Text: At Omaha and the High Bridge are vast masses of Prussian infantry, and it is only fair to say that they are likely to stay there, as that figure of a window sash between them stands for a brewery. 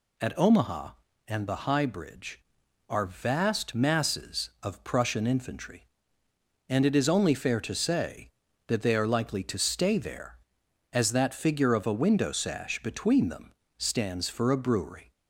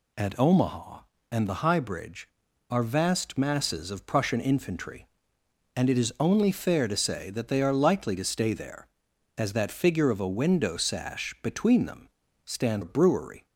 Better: first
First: pauses between "them" and "stands"; slight; at 13.5 s; 0.26 s long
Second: pauses between "them" and "stands"; slight; at 12.0 s; 0.36 s long // skips "for"; at 12.8 s

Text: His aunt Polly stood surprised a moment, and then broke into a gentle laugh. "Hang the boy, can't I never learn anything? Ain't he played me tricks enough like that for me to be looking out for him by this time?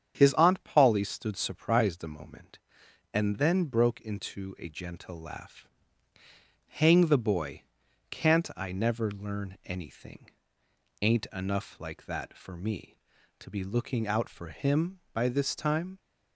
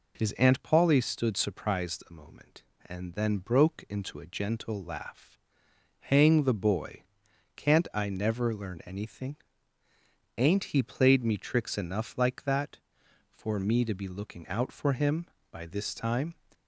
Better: second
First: starts louder than the rest; strong; until 1.1 s; 8 dB // skips "he played me tricks"; at 11.2 s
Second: none

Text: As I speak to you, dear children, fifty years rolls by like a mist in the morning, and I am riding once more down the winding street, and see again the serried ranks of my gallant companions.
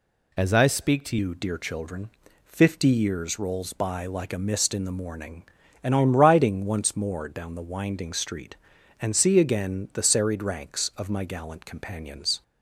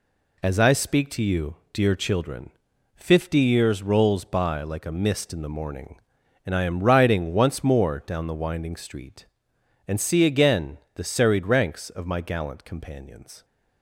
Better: second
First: changes voice at "you"; from 1.1 s on; 11.3 s long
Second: none

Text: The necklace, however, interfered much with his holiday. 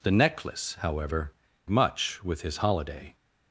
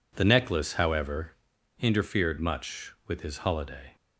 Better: second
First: skips "interfered"; at 1.5 s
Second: none

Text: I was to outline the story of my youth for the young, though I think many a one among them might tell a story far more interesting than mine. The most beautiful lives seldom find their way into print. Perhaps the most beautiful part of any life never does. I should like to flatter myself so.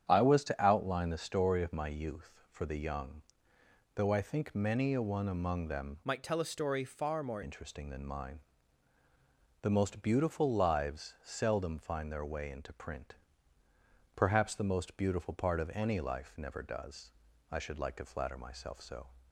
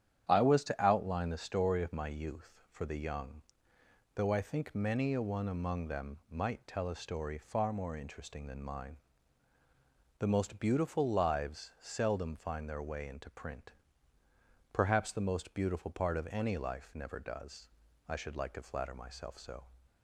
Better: second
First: starts louder than the rest; strong; until 1.0 s; 9 dB // changes voice from "might" to "more"; from 6.0 to 7.4 s; 1.4 s long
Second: starts louder than the rest; strong; until 1.2 s; 9.5 dB

